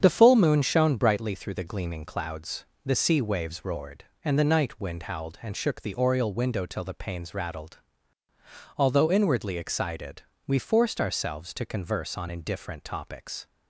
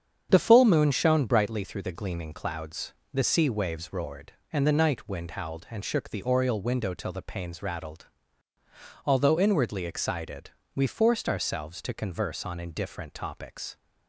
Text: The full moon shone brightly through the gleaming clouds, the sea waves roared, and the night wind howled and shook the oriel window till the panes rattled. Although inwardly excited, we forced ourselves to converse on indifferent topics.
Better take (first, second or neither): neither